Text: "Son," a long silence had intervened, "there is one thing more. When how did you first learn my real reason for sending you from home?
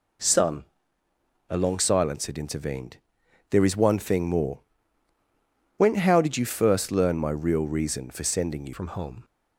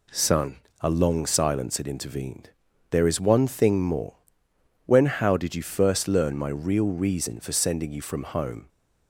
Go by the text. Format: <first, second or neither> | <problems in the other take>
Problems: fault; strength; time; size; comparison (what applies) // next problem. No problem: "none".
second | changes voice at "from"; from 8.7 s on; 0.5 s long